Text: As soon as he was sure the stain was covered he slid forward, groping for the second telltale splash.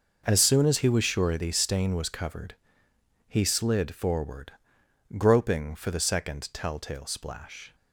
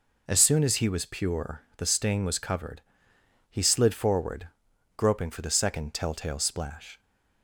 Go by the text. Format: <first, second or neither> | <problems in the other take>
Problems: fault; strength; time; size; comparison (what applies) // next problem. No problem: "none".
first | says "pure" for "sure"; at 1.0 s // pauses between "covered" and "he"; noticeable; at 2.8 s; 0.68 s long; noticeable in the first